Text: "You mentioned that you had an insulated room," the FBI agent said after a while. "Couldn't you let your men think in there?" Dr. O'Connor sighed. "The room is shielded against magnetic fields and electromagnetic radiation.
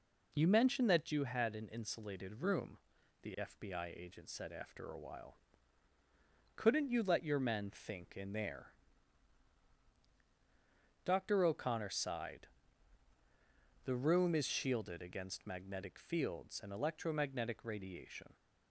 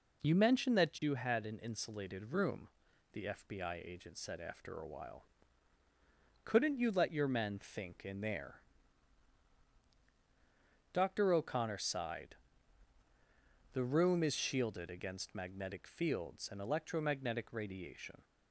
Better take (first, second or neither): neither